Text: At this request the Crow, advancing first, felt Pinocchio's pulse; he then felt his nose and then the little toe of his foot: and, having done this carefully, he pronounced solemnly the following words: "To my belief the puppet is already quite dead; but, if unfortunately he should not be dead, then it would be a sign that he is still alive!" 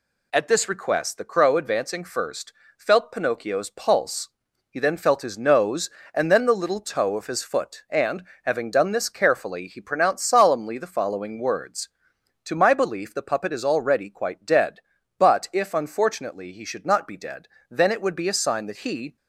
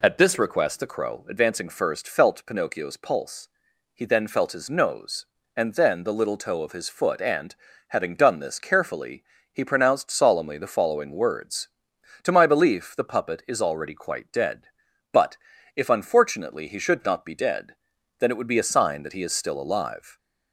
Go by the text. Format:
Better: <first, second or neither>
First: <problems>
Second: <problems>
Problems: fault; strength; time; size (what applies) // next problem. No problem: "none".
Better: second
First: stops before "is still alive"; at 19.1 s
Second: none